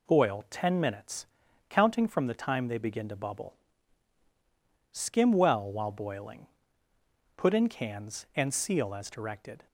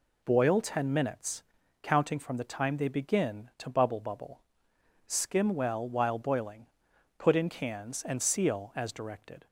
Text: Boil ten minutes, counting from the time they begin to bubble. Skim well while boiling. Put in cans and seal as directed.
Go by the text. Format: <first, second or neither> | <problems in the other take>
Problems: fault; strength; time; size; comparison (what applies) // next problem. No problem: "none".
first | says "bubble" twice; at 3.9 s